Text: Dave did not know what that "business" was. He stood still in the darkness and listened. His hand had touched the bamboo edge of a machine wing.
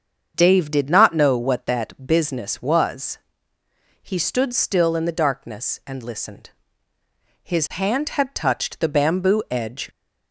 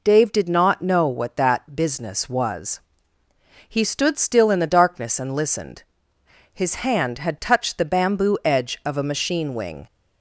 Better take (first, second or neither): second